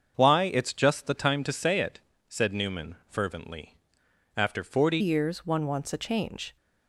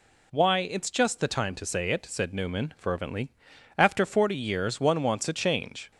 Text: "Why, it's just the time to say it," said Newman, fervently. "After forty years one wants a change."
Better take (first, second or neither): second